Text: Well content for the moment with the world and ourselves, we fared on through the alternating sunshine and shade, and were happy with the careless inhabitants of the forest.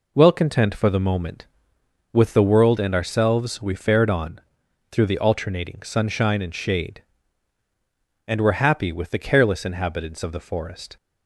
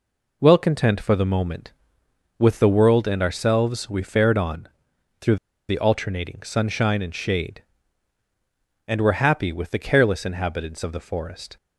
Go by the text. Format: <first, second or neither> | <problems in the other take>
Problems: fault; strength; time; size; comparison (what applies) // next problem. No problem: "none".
first | pauses between "on" and "through"; noticeable; at 4.6 s; 0.50 s long; noticeable in the first // pauses between "through" and "the"; slight; at 5.3 s; 0.33 s long